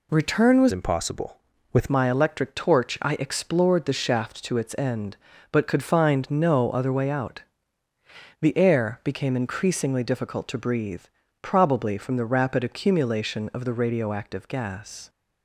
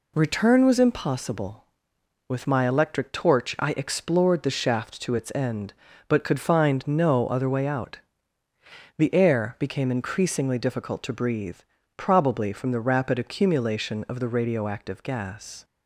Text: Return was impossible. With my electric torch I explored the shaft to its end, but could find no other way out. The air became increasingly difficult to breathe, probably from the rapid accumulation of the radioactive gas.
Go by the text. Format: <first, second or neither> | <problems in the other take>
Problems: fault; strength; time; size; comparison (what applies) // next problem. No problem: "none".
second | changes voice from "impossible" to "With"; from 0.7 to 1.8 s; 1.1 s long